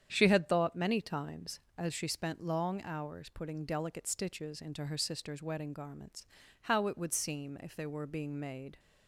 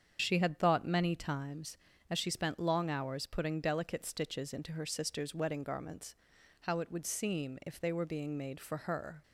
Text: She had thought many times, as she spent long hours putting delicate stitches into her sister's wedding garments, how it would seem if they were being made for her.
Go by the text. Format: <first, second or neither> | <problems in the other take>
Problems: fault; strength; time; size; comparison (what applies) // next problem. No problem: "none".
second | starts louder than the rest; strong; until 1.1 s; 9 dB; strong in the second // stops before "for her"; at 8.7 s